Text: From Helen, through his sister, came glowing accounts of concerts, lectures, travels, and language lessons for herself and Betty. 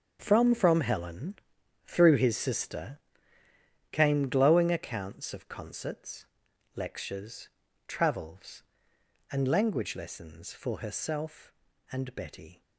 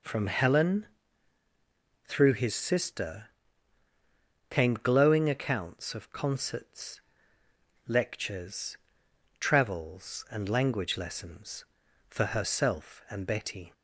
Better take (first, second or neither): second